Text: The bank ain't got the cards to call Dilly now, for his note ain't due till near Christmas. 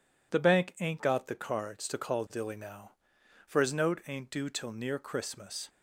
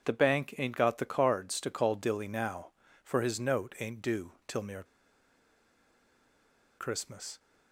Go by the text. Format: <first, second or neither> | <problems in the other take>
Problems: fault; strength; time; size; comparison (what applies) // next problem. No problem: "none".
first | pauses between "due" and "till"; slight; at 4.3 s; 0.16 s long // pauses between "near" and "Christmas"; strong; at 4.8 s; 1.9 s long